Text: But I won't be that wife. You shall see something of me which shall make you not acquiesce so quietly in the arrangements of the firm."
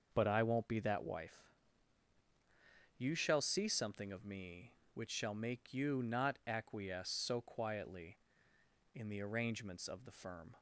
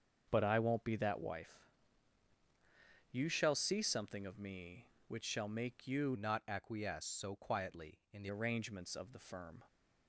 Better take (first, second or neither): first